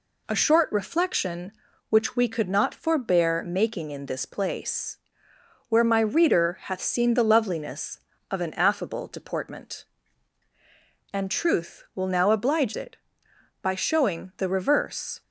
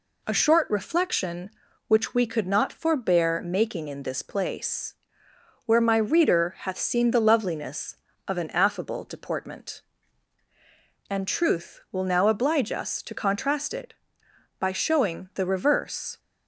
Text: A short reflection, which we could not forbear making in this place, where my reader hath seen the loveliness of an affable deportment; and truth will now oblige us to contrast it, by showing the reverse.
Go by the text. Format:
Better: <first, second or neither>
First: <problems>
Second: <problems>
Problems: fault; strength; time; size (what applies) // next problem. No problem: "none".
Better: second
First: skips "us to contrast"; at 12.7 s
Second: none